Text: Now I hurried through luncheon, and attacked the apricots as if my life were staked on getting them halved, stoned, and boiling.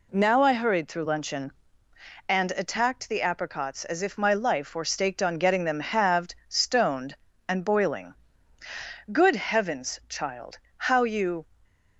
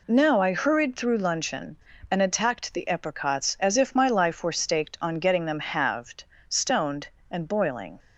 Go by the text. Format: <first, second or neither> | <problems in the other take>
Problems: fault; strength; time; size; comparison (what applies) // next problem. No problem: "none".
second | goes on to say "Good Heavens child how you"; strong; from 9.1 s on; 2.3 s long